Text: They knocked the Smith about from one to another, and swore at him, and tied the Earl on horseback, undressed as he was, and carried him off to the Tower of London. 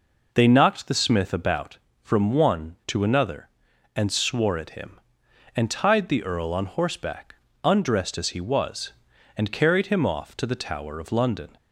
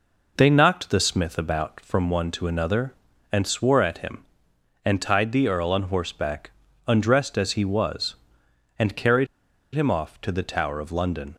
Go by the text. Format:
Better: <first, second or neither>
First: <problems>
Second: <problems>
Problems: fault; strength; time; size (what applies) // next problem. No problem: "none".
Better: first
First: none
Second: pauses between "carried" and "him"; noticeable; at 9.2 s; 0.48 s long